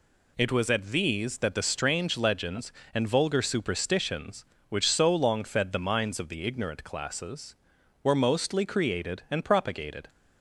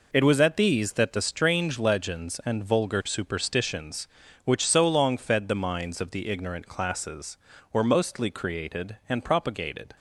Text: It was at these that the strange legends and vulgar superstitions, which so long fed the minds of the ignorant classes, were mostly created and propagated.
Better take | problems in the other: neither | none

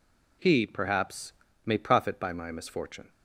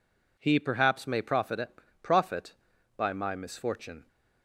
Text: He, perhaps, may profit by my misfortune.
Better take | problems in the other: first | says "profit" twice; at 2.0 s

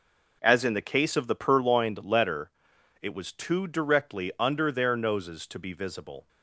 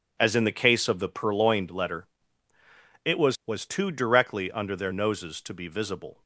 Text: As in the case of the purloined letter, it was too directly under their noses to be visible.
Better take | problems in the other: first | says "was" twice; at 3.4 s

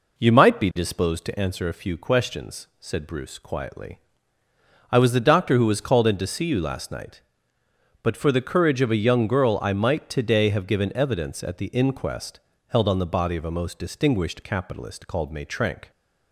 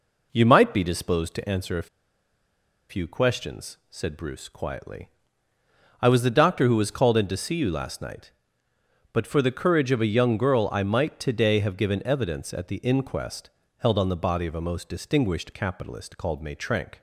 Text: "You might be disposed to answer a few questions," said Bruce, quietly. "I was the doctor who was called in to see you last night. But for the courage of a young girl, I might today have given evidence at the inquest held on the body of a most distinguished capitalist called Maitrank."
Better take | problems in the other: first | pauses between "a" and "few"; at 1.8 s; 1.0 s long // pauses between "inquest" and "held"; slight; at 13.4 s; 0.30 s long; slight in the first

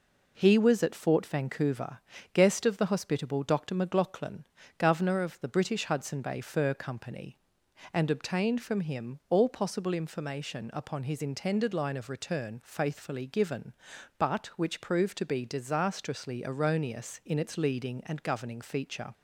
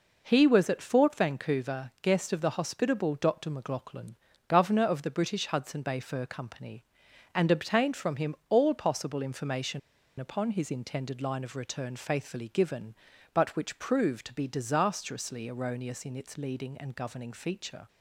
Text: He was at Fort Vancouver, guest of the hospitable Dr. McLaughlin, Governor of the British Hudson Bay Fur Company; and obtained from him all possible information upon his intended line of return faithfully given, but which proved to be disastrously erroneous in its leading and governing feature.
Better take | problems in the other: first | pauses between "information" and "upon"; at 9.7 s; 0.39 s long

